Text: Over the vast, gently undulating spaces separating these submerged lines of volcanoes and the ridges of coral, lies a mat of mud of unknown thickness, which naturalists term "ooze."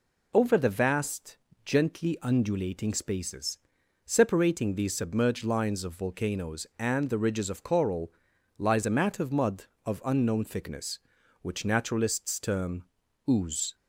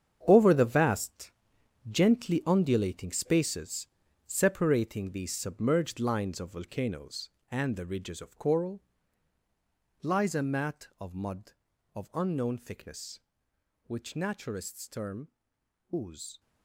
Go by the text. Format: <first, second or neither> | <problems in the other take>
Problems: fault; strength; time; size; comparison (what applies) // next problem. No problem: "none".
first | gets quieter; strong; throughout; 11.5 dB // pauses between "spaces" and "separating"; at 3.8 s; 0.40 s long; noticeable in the first // pauses between "term" and "ooze"; noticeable; at 15.2 s; 0.62 s long; also in the first